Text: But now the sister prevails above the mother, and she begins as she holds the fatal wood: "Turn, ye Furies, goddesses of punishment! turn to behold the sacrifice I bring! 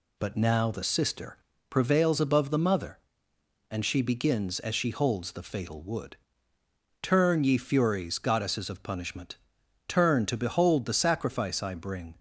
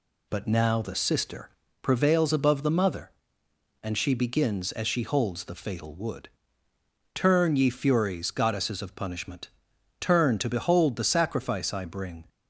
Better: neither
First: pauses between "sister" and "prevails"; slight; at 1.3 s; 0.32 s long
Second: pauses between "sister" and "prevails"; slight; at 1.4 s; 0.32 s long

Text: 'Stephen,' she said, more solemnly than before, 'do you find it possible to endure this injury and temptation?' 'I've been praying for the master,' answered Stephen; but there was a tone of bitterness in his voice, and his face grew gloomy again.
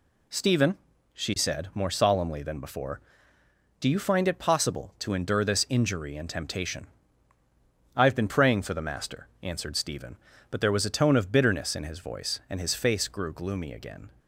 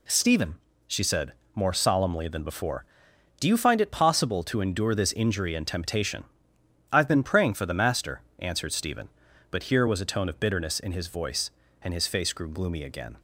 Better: first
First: none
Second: says "here" for "there"; at 9.6 s

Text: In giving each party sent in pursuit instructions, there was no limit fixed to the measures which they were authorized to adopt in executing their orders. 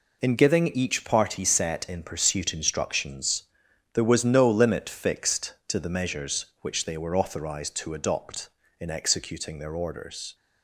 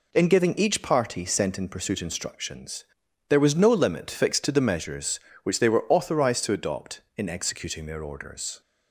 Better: second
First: says "set" for "sent"; at 1.4 s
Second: none

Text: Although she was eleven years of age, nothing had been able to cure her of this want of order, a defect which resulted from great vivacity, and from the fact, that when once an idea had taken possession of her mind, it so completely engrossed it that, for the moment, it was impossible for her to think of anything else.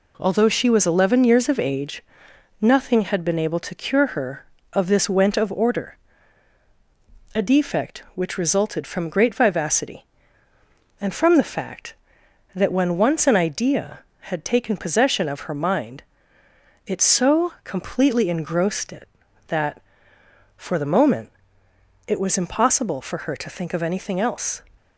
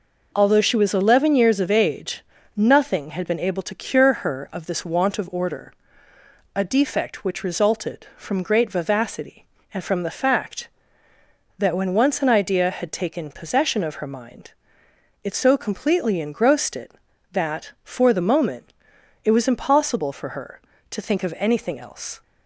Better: second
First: says "went" for "want"; at 5.0 s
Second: none

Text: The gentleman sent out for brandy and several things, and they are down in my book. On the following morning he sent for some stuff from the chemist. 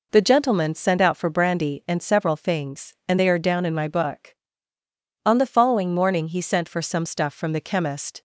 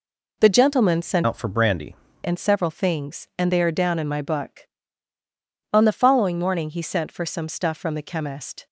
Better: first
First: none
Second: changes voice from "out" to "brandy"; from 1.2 to 1.9 s; 0.7 s long

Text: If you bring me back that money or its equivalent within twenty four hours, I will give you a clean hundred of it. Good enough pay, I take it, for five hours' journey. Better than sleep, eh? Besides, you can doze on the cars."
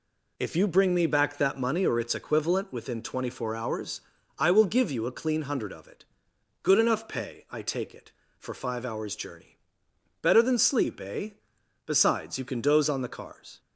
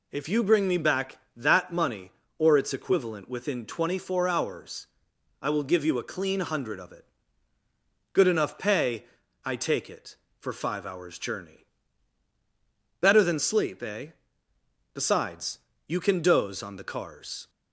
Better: neither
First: none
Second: none

